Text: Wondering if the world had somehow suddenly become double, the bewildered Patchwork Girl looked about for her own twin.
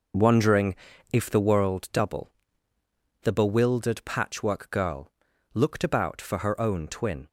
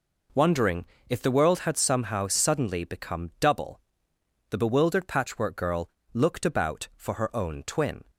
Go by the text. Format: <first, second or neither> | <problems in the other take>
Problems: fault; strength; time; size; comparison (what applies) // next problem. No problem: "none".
second | pauses between "Wondering" and "if"; slight; at 0.7 s; 0.36 s long; slight in the second // skips "had somehow suddenly become"; at 1.9 s // pauses between "Girl" and "looked"; at 5.1 s; 0.42 s long; slight in the second